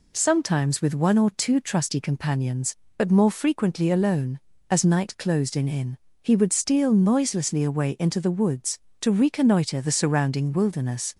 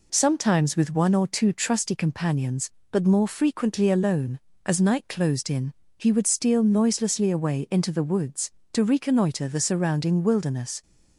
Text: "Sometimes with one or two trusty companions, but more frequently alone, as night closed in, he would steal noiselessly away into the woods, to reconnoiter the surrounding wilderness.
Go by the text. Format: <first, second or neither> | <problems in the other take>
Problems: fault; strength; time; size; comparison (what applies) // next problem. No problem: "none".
second | says "in" twice; at 5.6 s